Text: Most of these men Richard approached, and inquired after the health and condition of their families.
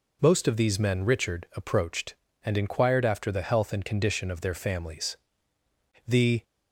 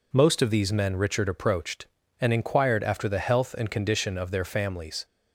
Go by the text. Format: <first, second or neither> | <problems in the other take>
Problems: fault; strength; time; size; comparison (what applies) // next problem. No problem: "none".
second | goes on to say "The"; slight; from 6.0 s on; 0.36 s long